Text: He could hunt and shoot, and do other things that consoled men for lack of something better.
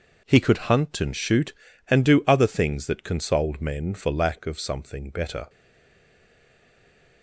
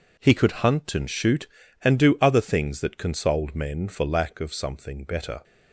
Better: second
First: stays silent after the last word; noticeable; from 5.4 s on; 1.8 s long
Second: none

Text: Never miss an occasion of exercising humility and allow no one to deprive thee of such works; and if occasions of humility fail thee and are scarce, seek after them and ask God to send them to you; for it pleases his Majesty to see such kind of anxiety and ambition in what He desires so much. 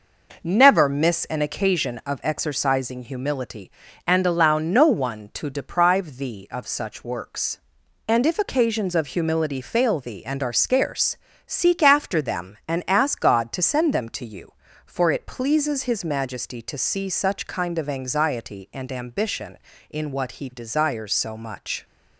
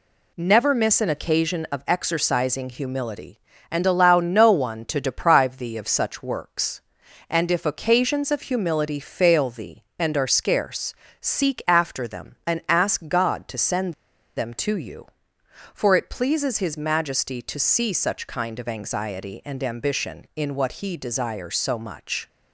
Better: first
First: none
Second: pauses between "send" and "them"; at 13.9 s; 0.43 s long

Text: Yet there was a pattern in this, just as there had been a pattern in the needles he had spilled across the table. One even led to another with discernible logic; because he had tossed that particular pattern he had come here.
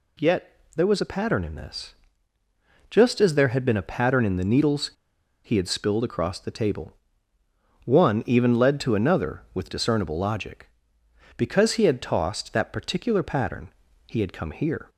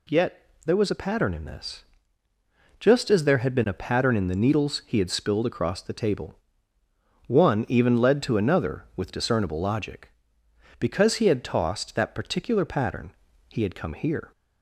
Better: second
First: pauses between "Yet" and "there"; slight; at 0.5 s; 0.24 s long // pauses between "needles" and "he"; noticeable; at 4.9 s; 0.54 s long // pauses between "pattern" and "he"; at 13.6 s; 0.38 s long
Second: pauses between "Yet" and "there"; slight; at 0.4 s; 0.24 s long // pauses between "pattern" and "he"; at 13.1 s; 0.38 s long

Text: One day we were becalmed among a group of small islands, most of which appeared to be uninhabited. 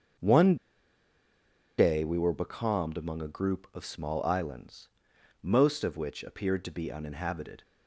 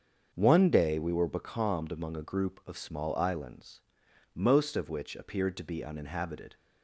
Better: second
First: starts louder than the rest; until 2.4 s; 7 dB // pauses between "One" and "day"; at 0.5 s; 1.2 s long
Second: starts louder than the rest; until 1.3 s; 6.5 dB

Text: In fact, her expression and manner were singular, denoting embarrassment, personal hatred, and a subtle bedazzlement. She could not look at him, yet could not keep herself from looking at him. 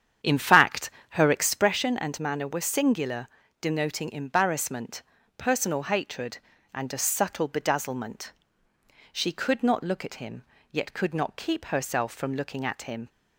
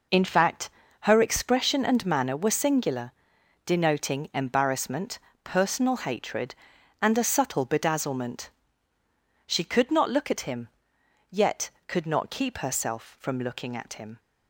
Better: second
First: starts louder than the rest; strong; until 1.7 s; 8.5 dB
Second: none

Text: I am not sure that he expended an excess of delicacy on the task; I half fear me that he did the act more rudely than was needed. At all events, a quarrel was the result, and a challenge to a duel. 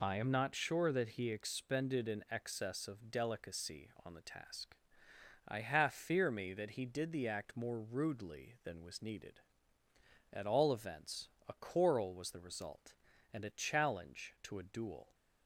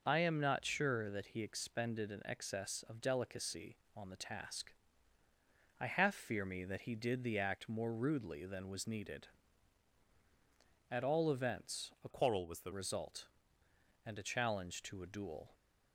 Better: first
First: none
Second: changes voice from "quarrel" to "the"; from 12.1 to 12.7 s; 0.6 s long

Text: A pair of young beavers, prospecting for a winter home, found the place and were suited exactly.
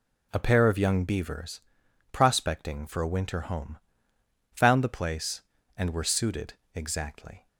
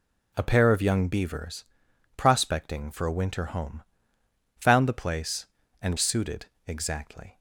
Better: first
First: pauses between "suited" and "exactly"; slight; at 6.5 s; 0.22 s long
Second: skips "were"; at 5.9 s // pauses between "suited" and "exactly"; slight; at 6.4 s; 0.22 s long

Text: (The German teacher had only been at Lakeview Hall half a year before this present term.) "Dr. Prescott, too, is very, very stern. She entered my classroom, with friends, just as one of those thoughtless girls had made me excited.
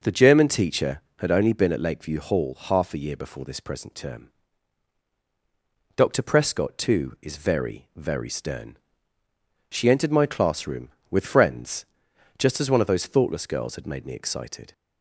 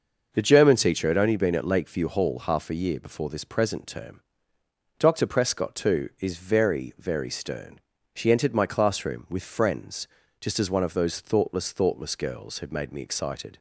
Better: first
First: none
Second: starts louder than the rest; noticeable; until 1.3 s; 6 dB // says "thoughtless" twice; at 11.7 s

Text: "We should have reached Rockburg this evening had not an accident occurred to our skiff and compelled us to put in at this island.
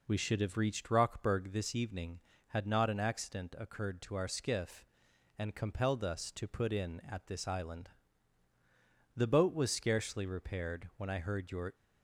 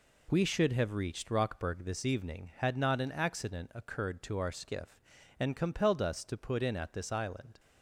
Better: second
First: goes on to say "The boat was scarcely repaired when I heard your"; strong; from 9.1 s on; 2.5 s long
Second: none

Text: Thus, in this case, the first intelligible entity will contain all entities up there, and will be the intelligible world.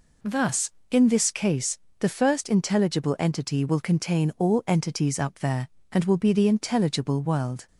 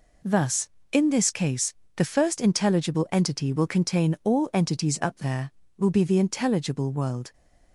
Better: first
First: none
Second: skips "and"; at 5.6 s

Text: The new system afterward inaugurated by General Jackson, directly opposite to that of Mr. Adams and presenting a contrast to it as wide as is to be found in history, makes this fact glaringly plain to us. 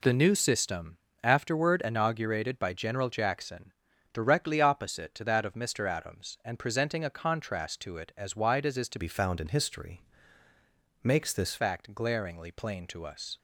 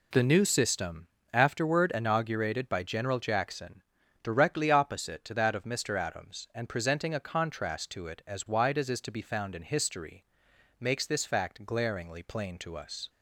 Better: second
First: pauses between "system" and "afterward"; slight; at 0.9 s; 0.26 s long // changes voice from "be" to "this"; from 8.9 to 11.5 s; 2.6 s long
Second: pauses between "system" and "afterward"; slight; at 1.0 s; 0.26 s long

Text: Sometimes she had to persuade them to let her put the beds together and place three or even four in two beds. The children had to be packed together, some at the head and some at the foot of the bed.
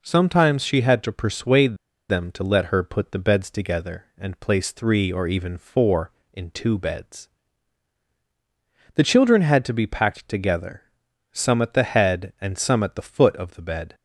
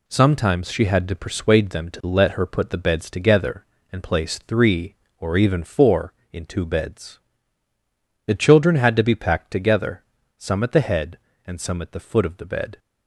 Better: second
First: pauses between "persuade" and "them"; slight; at 1.7 s; 0.33 s long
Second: none

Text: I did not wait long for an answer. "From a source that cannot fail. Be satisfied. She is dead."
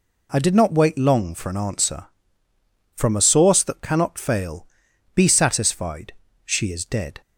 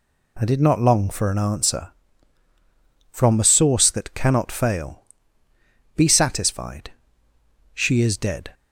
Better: first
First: none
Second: skips "wait"; at 0.7 s

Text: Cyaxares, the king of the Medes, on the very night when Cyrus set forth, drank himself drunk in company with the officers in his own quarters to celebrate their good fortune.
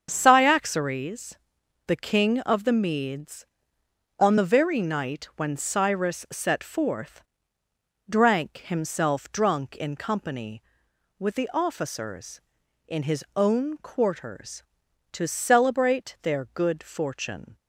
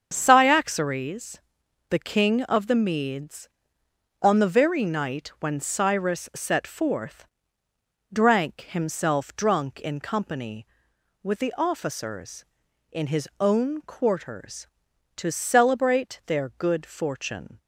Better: neither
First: starts louder than the rest; strong; until 1.1 s; 7 dB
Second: starts louder than the rest; strong; until 1.1 s; 7 dB

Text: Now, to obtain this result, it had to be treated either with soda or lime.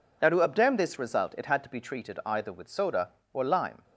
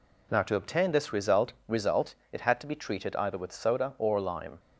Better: first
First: none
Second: says "result" twice; at 1.6 s

